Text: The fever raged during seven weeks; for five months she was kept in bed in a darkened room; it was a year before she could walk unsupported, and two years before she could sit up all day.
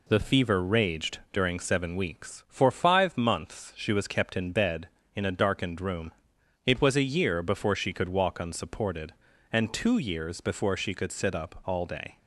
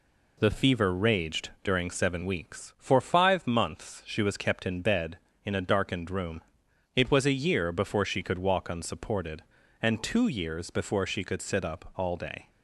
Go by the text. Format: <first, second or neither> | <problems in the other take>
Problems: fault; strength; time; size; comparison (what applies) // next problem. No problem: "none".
neither | pauses between "raged" and "during"; slight; the same in both